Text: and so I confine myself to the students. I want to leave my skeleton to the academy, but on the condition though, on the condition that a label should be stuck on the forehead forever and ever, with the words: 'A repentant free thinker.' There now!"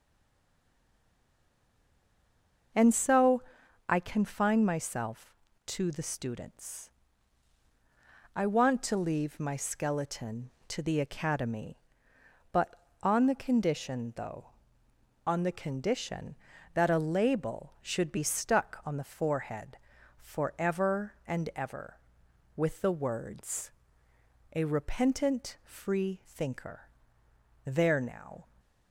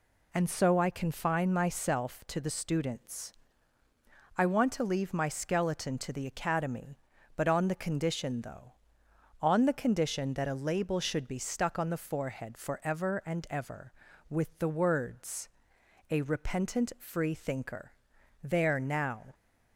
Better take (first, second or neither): second